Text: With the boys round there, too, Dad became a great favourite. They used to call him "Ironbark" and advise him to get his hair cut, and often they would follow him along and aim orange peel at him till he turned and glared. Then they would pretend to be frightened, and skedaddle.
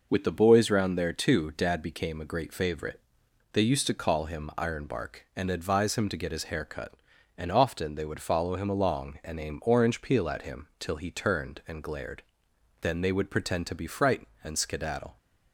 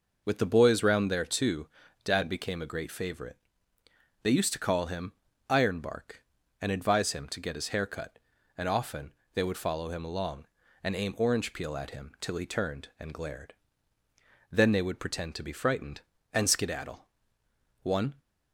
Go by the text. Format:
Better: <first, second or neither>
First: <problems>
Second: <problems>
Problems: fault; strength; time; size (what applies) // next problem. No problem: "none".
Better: first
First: none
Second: pauses between "him" and "Ironbark"; slight; at 5.1 s; 0.34 s long // pauses between "often" and "they"; slight; at 9.1 s; 0.22 s long // goes on to say "One"; slight; from 17.8 s on; 0.38 s long